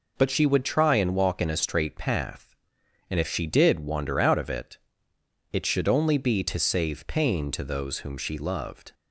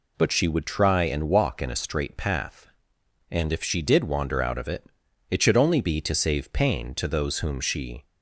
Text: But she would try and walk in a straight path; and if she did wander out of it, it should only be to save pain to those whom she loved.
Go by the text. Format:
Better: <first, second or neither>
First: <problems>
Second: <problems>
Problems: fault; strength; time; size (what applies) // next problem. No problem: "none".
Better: first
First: none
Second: stops before "loved"; at 8.0 s